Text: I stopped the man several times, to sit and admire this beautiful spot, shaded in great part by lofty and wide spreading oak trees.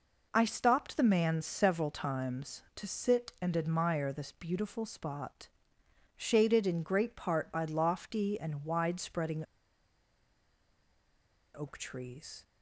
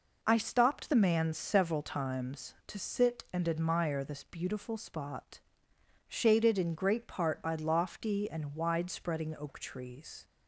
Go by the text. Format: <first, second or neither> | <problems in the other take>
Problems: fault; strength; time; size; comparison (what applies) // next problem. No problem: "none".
second | pauses between "spreading" and "oak"; strong; at 9.4 s; 2.1 s long